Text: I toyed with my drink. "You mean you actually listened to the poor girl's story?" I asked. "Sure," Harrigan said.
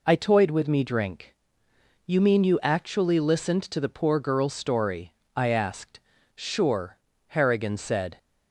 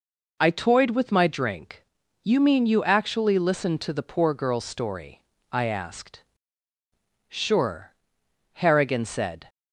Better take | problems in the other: second | says "me" for "my"; at 0.6 s

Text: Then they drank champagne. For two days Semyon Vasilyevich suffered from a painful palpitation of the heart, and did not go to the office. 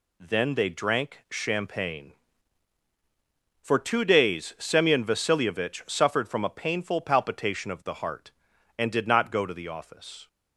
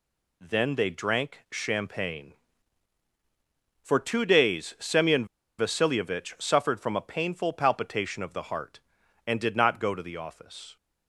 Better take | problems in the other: first | pauses between "Semyon" and "Vasilyevich"; slight; at 5.2 s; 0.33 s long

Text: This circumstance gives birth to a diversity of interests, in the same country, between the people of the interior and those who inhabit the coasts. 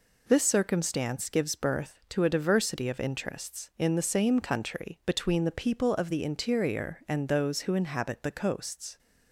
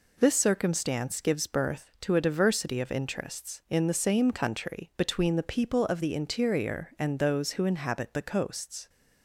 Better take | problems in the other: neither | none

